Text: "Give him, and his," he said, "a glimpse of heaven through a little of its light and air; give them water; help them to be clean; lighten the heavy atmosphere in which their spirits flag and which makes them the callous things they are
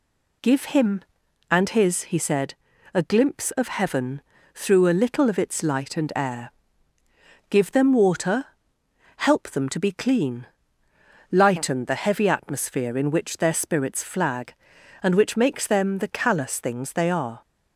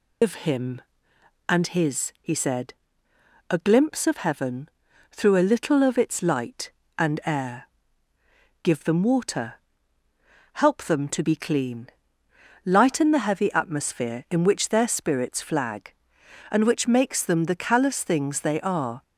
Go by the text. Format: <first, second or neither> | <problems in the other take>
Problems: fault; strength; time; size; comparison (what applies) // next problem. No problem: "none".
first | loses the start of "Give"; at 0.2 s; 135 ms // pauses between "heaven" and "through"; at 4.6 s; 0.42 s long; slight in the first